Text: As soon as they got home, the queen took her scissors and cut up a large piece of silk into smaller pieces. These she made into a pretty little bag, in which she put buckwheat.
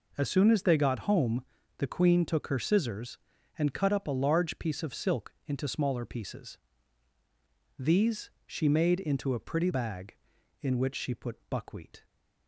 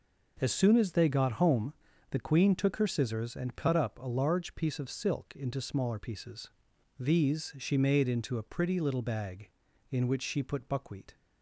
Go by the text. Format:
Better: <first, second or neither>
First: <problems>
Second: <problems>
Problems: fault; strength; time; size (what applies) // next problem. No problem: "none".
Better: second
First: pauses between "These" and "she"; slight; at 8.3 s; 0.16 s long // skips "little"; at 9.7 s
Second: none